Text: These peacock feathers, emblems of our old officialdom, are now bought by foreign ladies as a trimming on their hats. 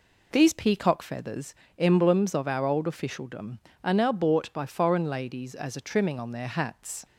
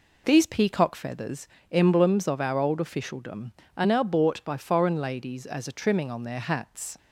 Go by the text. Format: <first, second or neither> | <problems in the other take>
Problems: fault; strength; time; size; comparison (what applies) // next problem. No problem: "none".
neither | none